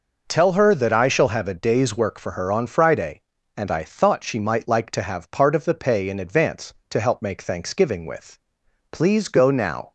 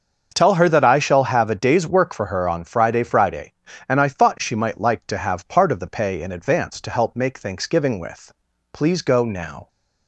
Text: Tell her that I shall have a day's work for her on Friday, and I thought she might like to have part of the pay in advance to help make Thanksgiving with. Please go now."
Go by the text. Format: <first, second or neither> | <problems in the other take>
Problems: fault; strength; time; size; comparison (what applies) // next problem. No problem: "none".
first | starts louder than the rest; until 1.3 s; 6.5 dB // says "Friday" twice; at 3.0 s